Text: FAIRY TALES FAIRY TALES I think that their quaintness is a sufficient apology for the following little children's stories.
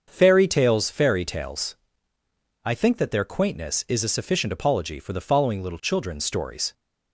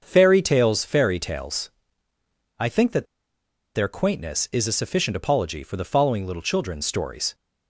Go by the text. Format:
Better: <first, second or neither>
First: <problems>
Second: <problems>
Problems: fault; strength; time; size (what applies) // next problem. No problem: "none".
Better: first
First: starts louder than the rest; until 1.1 s; 6.5 dB // pauses between "TALES" and "I"; noticeable; at 1.7 s; 0.90 s long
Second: starts louder than the rest; until 1.0 s; 6.5 dB // pauses between "TALES" and "I"; noticeable; at 1.6 s; 0.90 s long // pauses between "that" and "their"; noticeable; at 3.0 s; 0.69 s long